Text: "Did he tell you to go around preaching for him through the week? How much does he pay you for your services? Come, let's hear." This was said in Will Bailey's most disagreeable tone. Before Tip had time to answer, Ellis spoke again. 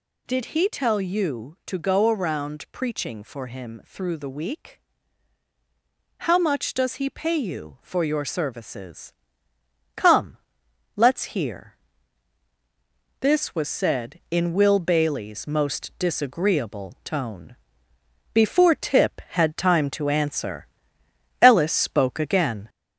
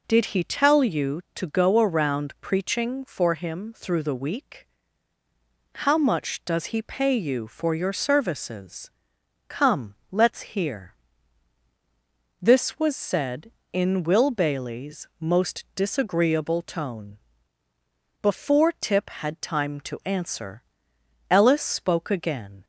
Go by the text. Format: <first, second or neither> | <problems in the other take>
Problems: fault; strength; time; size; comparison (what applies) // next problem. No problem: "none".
second | gets louder; slight; throughout; 2.5 dB